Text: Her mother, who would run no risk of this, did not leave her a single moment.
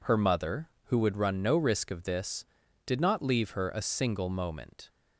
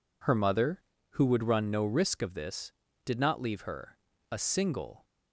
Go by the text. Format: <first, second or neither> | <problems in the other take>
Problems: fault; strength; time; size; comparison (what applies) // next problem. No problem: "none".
first | pauses between "her" and "a"; slight; at 3.9 s; 0.32 s long // stops before "moment"; at 5.0 s